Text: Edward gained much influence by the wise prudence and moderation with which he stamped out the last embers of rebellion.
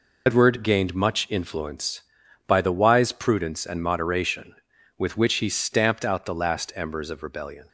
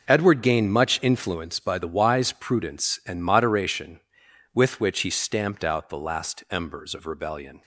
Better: second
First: loses the start of "Edward"; at 0.2 s; 95 ms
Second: none

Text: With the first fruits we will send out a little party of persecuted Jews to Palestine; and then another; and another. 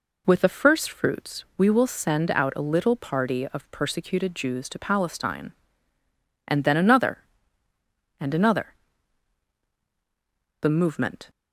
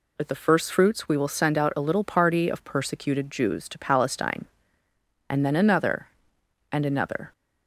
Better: second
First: goes on to say "The movement"; noticeable; from 10.6 s on; 0.68 s long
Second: none

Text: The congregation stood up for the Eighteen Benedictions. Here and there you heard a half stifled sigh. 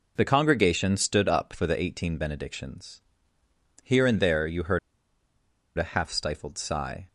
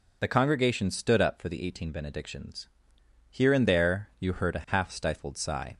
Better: second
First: pauses between "heard" and "a"; noticeable; at 4.7 s; 0.97 s long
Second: none

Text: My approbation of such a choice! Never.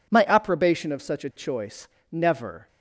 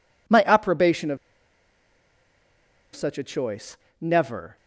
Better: first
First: none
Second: pauses between "of" and "such"; strong; at 1.1 s; 1.7 s long

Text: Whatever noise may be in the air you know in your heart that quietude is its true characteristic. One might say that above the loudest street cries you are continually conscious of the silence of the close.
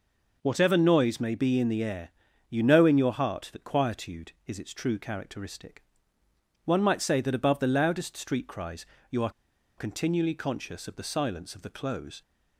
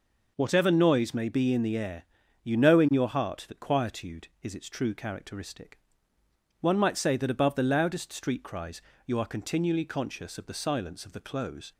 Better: second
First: pauses between "air" and "you"; at 2.0 s; 0.38 s long // pauses between "cries" and "you"; slight; at 8.8 s; 0.24 s long // pauses between "are" and "continually"; noticeable; at 9.2 s; 0.47 s long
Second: pauses between "air" and "you"; at 2.0 s; 0.38 s long // pauses between "cries" and "you"; slight; at 8.8 s; 0.24 s long

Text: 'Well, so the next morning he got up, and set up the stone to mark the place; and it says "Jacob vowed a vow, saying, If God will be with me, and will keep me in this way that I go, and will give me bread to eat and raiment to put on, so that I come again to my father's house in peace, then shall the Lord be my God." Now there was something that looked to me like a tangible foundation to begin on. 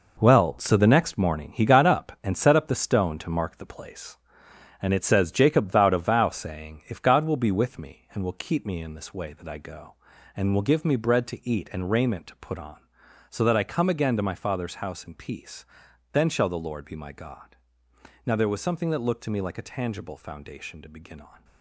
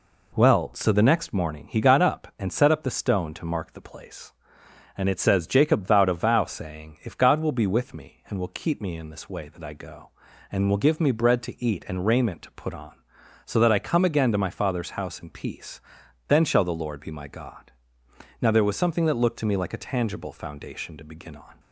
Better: second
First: gets quieter; strong; throughout; 9 dB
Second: none

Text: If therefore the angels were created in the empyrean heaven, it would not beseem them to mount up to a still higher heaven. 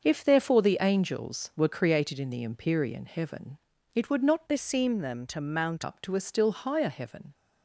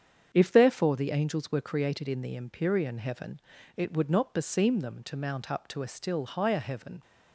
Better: second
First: starts louder than the rest; until 1.0 s; 6.5 dB // changes voice from "beseem" to "mount"; from 4.4 to 5.8 s; 1.4 s long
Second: starts louder than the rest; strong; until 1.3 s; 7.5 dB

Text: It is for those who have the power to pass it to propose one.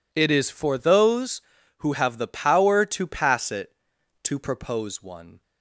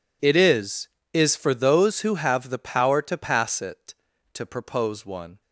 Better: first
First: none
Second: says "is" twice; at 1.1 s

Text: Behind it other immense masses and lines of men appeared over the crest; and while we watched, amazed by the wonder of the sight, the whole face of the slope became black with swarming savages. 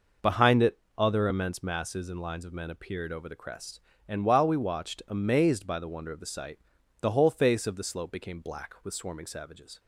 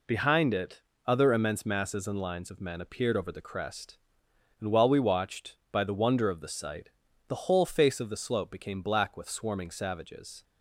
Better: first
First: pauses between "it" and "other"; slight; at 0.7 s; 0.20 s long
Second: pauses between "it" and "other"; slight; at 0.8 s; 0.26 s long // skips "amazed"; at 5.6 s

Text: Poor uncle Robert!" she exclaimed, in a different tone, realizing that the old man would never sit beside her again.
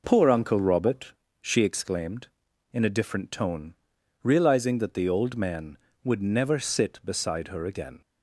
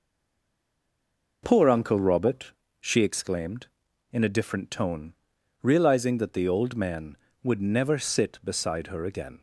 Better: first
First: none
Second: stays silent before the first word; noticeable; until 1.4 s; 1.4 s long

